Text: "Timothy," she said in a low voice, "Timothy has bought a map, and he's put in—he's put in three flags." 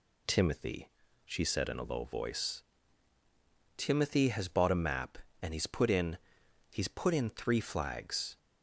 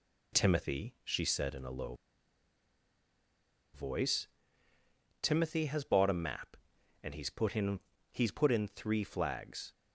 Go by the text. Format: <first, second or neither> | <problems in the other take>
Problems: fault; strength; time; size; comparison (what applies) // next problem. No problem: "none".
first | pauses between "low" and "voice"; strong; at 1.9 s; 1.7 s long